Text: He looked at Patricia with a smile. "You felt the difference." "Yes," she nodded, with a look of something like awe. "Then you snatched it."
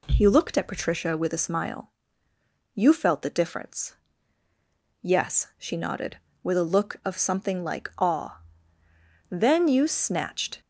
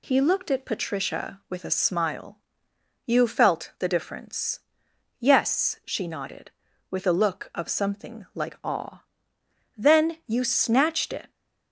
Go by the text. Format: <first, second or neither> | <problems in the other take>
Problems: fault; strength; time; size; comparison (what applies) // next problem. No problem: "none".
second | stops before "it"; at 10.6 s